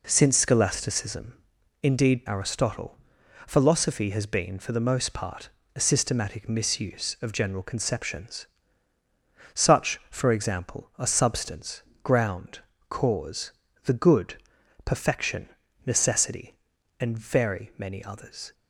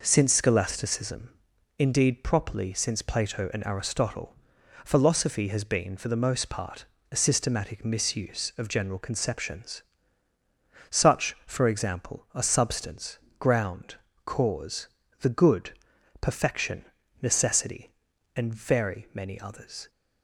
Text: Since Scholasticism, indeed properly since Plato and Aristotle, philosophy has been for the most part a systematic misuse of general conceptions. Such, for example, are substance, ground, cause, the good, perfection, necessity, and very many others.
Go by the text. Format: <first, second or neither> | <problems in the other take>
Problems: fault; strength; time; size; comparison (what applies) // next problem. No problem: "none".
second | skips "properly since Plato and"; at 2.2 s // pauses between "part" and "a"; slight; at 5.4 s; 0.26 s long; slight in the second